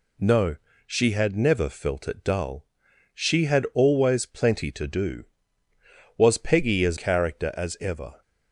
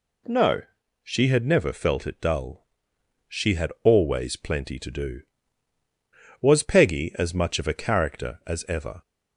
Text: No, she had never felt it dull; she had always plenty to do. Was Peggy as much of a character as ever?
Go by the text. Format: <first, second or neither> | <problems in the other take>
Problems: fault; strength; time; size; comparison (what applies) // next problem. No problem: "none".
second | skips "much of a"; at 6.9 s